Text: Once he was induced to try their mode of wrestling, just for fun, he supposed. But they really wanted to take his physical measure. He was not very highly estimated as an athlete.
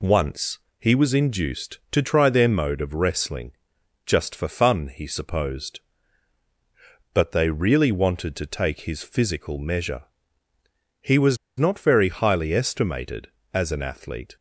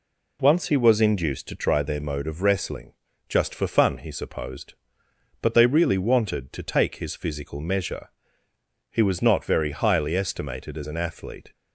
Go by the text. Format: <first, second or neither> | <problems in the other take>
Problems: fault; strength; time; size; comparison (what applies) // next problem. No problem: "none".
second | pauses between "Once" and "he"; slight; at 0.5 s; 0.22 s long // pauses between "was" and "not"; slight; at 11.3 s; 0.20 s long